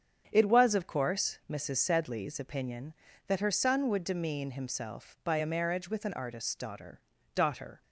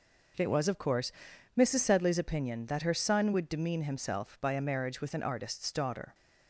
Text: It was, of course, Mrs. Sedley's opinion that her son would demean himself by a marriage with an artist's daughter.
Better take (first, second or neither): second